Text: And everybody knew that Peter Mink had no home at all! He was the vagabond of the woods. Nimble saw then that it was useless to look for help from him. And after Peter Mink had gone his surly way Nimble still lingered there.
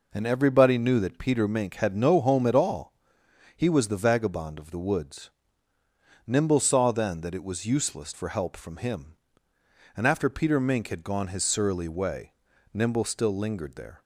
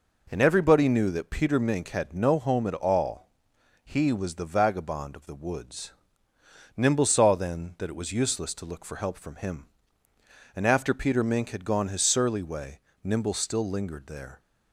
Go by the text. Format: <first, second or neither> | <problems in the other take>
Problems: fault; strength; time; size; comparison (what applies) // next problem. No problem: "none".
second | skips "to look"; at 8.1 s // pauses between "way" and "Nimble"; at 12.3 s; 0.40 s long; slight in the second